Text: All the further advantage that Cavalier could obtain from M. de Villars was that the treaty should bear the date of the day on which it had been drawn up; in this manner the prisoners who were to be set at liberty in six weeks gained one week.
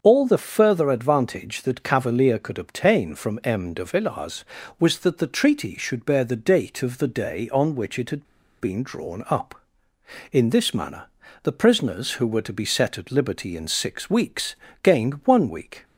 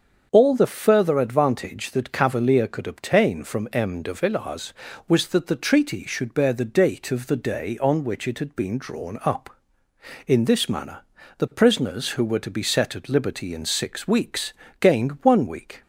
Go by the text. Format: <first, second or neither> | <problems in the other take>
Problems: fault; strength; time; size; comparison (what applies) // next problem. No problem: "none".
second | starts louder than the rest; until 1.0 s; 7 dB; also in the second // pauses between "had" and "been"; slight; at 8.2 s; 0.34 s long // pauses between "manner" and "the"; slight; at 11.0 s; 0.34 s long; slight in the second // pauses between "weeks" and "gained"; slight; at 14.5 s; 0.30 s long; slight in the second